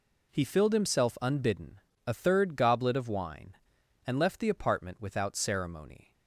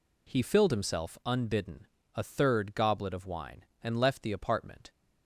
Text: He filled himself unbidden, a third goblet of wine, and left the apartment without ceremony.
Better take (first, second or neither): first